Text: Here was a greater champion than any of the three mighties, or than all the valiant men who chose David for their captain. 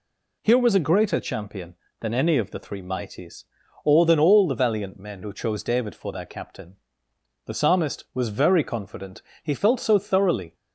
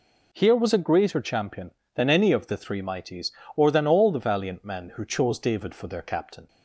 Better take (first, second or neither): second